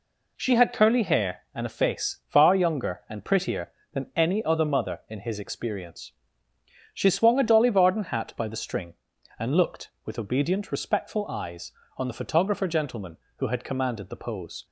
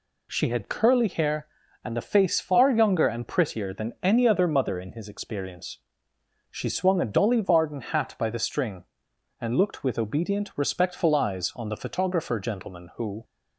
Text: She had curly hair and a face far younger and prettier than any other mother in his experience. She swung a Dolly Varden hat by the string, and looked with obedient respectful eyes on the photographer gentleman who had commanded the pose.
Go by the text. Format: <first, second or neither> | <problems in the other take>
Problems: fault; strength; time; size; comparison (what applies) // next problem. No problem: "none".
first | stops before "had commanded the pose"; at 13.2 s